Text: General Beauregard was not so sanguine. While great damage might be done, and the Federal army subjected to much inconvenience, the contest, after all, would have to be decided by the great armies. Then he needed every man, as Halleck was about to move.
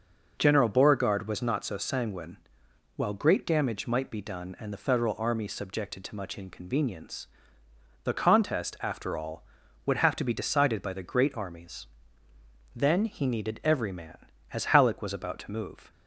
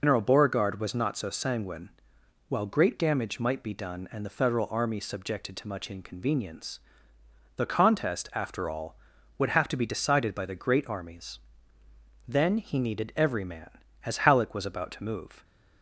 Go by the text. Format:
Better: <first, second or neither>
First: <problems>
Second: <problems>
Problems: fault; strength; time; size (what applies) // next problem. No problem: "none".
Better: first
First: none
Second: loses the start of "General"; at 0.0 s; 135 ms